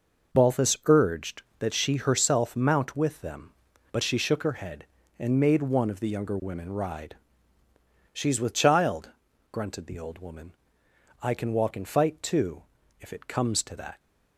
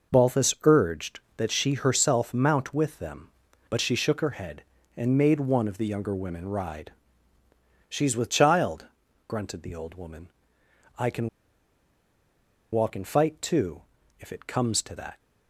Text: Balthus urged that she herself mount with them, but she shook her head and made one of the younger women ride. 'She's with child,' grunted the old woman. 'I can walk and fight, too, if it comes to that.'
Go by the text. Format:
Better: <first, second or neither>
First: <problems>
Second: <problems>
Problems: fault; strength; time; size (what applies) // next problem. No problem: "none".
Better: first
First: none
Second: pauses between "can" and "walk"; strong; at 11.2 s; 1.4 s long